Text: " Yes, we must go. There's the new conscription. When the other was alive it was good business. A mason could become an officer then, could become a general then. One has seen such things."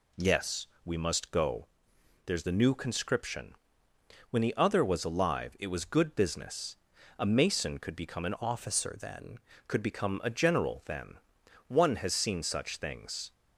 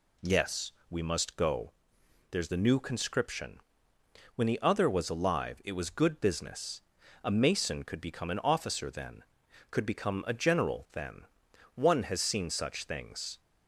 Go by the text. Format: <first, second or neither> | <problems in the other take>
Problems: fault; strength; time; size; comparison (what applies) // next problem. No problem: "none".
second | changes voice from "officer" to "then"; from 8.4 to 9.3 s; 0.9 s long